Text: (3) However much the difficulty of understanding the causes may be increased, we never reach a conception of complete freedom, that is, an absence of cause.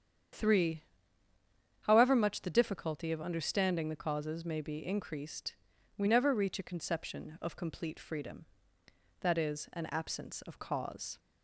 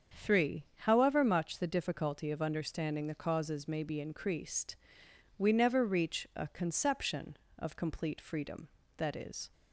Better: first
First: starts louder than the rest; strong; until 2.3 s; 8.5 dB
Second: starts louder than the rest; strong; until 1.3 s; 7 dB // stops before "an absence of cause"; at 9.5 s

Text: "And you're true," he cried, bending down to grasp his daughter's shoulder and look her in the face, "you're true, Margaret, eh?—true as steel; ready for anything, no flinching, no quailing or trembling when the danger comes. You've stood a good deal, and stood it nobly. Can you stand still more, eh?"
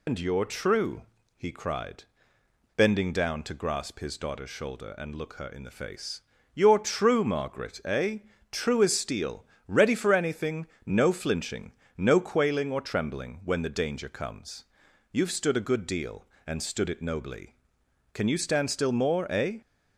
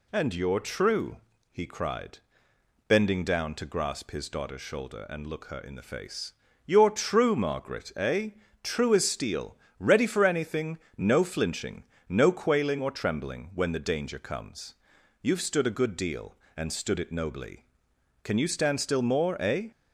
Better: second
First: loses the start of "And"; at 0.0 s; 115 ms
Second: none

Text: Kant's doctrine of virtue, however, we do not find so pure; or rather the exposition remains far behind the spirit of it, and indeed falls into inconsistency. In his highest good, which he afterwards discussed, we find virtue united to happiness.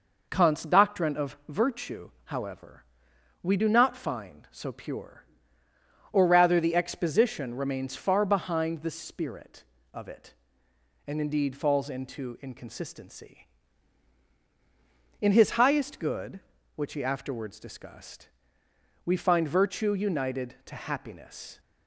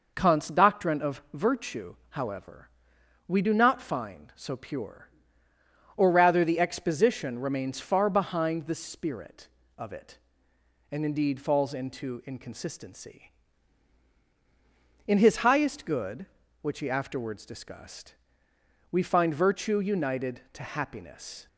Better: neither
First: none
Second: none

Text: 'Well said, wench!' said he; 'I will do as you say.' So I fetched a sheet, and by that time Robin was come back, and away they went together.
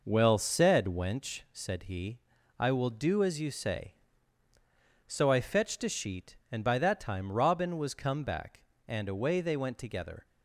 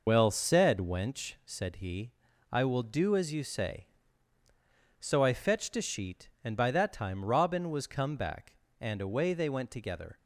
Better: first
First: none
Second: loses the start of "Well"; at 0.0 s; 100 ms

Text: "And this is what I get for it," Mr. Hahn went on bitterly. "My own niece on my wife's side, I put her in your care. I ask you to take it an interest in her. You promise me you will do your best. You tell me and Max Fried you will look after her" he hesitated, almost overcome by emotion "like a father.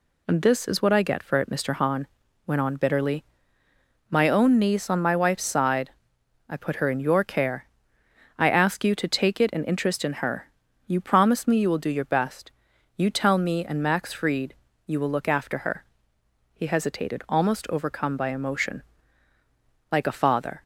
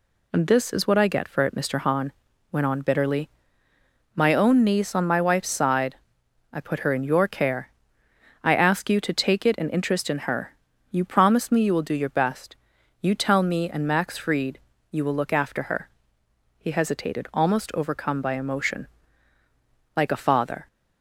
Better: neither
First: pauses between "Hahn" and "went"; at 2.0 s; 0.40 s long // pauses between "Fried" and "you"; slight; at 14.5 s; 0.32 s long // pauses between "her" and "he"; noticeable; at 15.8 s; 0.70 s long // pauses between "emotion" and "like"; at 18.8 s; 1.0 s long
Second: pauses between "Hahn" and "went"; at 2.1 s; 0.40 s long // pauses between "Fried" and "you"; slight; at 14.5 s; 0.32 s long // pauses between "her" and "he"; noticeable; at 15.8 s; 0.70 s long // pauses between "emotion" and "like"; at 18.8 s; 1.0 s long

